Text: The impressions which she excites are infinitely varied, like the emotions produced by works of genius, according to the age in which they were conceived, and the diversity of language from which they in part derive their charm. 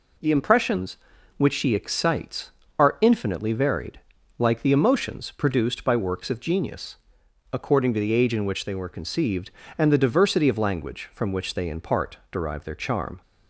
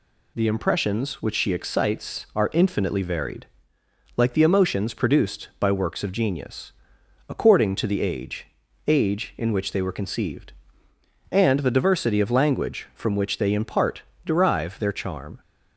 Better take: first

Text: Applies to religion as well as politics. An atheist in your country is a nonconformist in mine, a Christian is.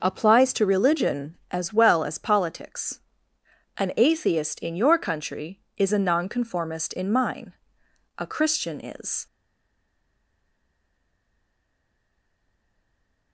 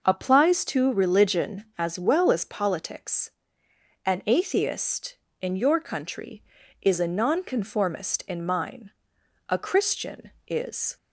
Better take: second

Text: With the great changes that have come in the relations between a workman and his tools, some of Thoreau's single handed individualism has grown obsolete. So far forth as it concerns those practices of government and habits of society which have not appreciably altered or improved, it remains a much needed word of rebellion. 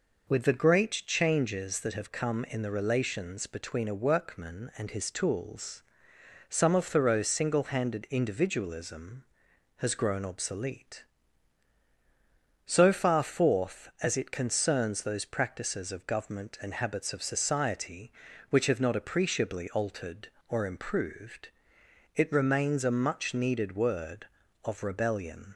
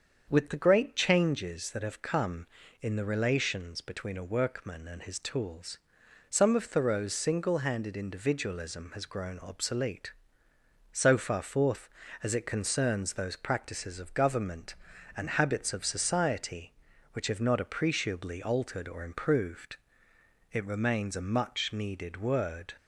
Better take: first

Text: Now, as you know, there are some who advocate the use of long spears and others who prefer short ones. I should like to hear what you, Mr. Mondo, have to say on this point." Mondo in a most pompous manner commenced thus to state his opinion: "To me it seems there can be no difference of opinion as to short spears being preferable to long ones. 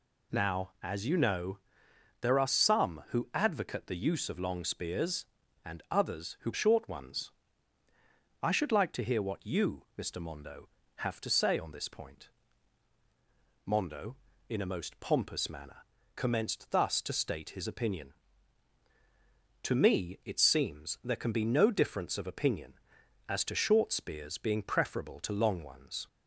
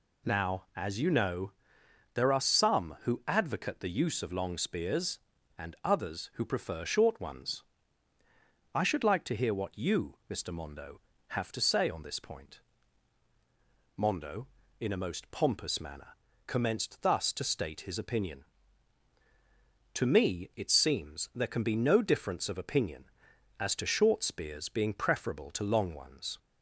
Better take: second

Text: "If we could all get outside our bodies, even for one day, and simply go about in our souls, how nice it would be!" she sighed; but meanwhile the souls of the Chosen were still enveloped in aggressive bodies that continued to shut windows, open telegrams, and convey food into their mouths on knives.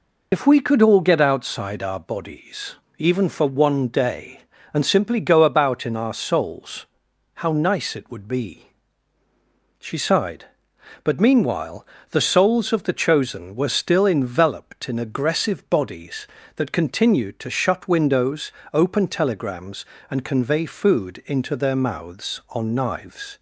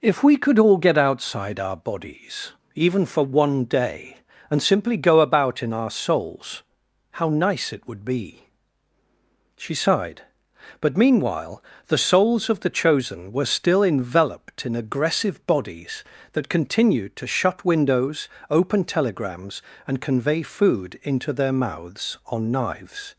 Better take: second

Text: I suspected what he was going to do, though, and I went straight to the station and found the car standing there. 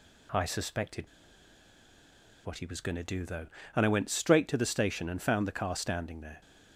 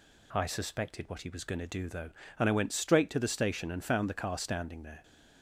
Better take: second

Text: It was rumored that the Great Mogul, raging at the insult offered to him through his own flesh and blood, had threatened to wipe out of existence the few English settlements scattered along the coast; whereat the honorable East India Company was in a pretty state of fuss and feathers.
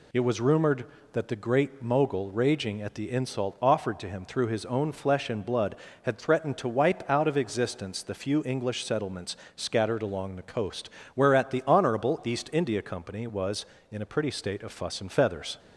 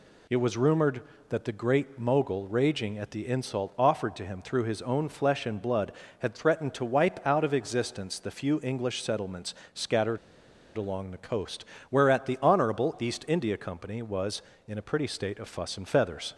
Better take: first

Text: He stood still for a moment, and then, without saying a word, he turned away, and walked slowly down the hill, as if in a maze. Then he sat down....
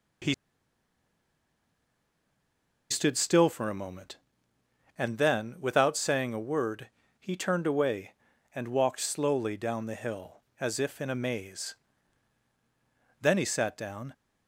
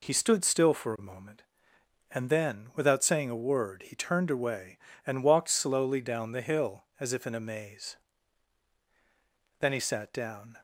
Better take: second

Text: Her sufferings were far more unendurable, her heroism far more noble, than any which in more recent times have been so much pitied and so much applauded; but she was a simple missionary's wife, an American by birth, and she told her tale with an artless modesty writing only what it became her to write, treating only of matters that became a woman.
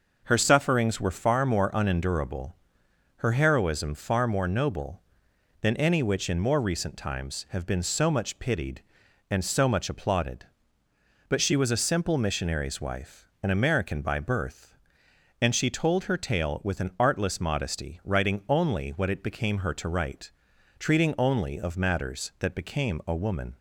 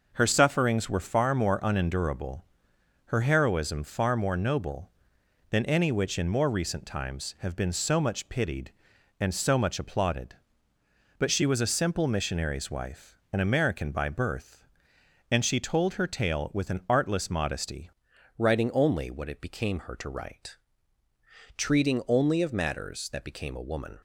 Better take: first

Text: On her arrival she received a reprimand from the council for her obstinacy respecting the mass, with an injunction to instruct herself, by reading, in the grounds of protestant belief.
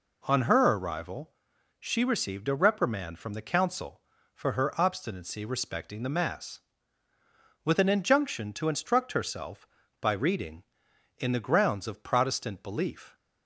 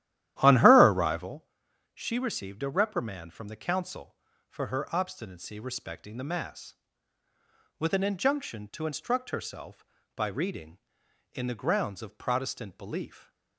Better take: first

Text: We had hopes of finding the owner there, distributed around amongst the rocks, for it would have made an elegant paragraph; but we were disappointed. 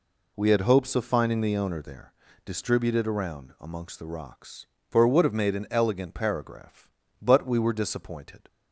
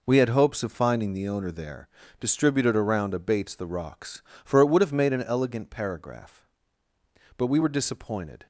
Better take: first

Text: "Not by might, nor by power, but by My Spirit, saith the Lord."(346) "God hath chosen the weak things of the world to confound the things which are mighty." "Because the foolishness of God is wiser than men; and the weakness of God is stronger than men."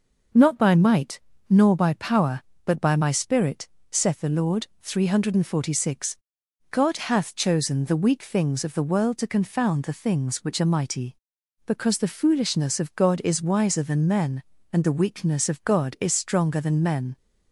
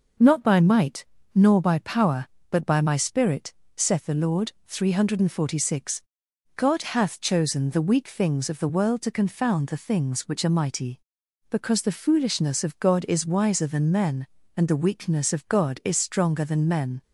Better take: neither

